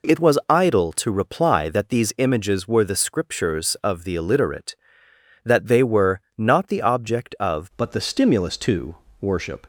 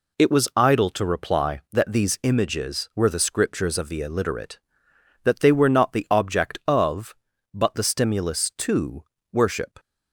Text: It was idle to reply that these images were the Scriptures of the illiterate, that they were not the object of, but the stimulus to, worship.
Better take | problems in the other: second | pauses between "were" and "not"; slight; at 6.2 s; 0.16 s long // changes voice at "but"; from 7.7 s on; 1.9 s long

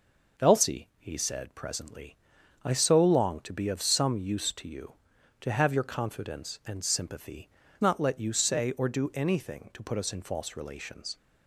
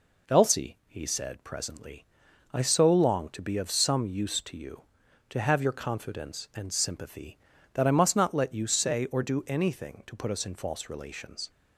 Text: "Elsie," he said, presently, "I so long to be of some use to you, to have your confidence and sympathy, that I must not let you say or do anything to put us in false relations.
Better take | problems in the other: second | skips "that I must"; at 7.6 s

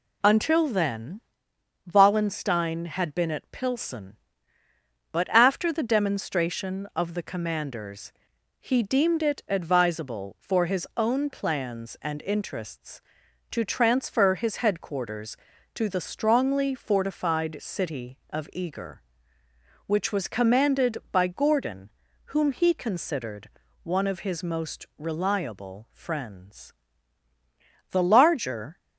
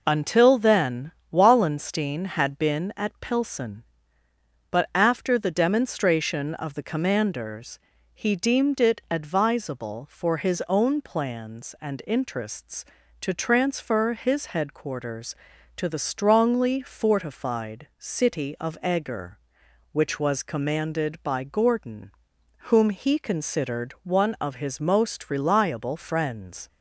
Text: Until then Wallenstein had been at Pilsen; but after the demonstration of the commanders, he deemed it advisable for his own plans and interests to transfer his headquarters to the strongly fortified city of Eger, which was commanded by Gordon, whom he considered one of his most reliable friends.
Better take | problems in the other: second | pauses between "then" and "Wallenstein"; noticeable; at 1.2 s; 0.72 s long; slight in the second // pauses between "considered" and "one"; slight; at 23.4 s; 0.36 s long // goes on to say "The larger"; noticeable; from 27.9 s on; 0.86 s long

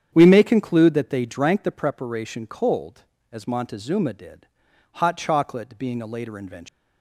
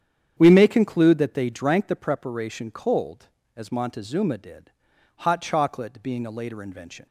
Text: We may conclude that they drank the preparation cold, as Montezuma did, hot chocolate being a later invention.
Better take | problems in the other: second | starts louder than the rest; strong; until 1.1 s; 8.5 dB; strong in the second // leaves "invention" unfinished; at 6.6 s; 130 ms

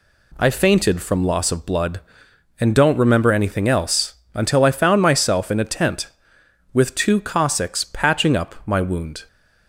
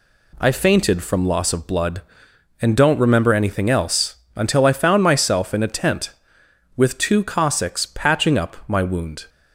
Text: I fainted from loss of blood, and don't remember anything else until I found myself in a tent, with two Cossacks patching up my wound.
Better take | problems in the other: neither | pauses between "else" and "until"; slight; the same in both

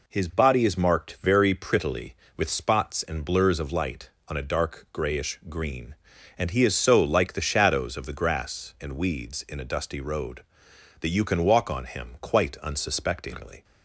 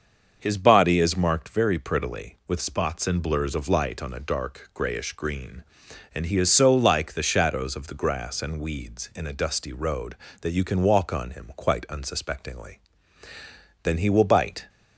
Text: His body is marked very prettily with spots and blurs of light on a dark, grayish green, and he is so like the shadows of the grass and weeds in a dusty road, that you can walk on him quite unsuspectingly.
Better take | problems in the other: first | starts louder than the rest; until 1.4 s; 6.5 dB // goes on to say "Then he will bite"; noticeable; from 13.8 s on; 0.86 s long

